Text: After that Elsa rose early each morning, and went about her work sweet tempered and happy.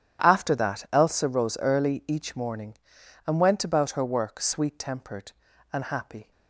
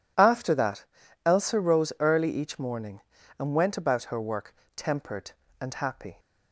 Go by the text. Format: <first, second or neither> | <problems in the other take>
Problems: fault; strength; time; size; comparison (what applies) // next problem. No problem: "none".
first | pauses between "that" and "Elsa"; at 0.8 s; 0.42 s long // skips "sweet"; at 4.6 s